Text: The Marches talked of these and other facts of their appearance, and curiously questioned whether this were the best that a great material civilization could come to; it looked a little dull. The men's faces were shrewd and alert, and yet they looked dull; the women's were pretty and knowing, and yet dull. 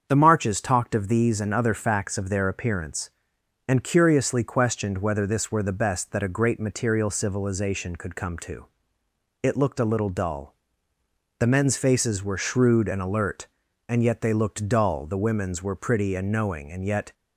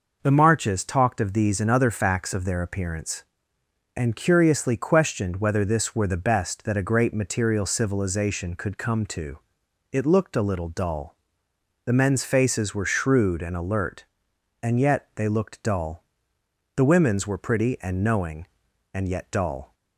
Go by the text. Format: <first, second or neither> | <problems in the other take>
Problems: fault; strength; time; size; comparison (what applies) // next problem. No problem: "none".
second | starts louder than the rest; strong; until 1.1 s; 7 dB // stops before "dull"; at 17.1 s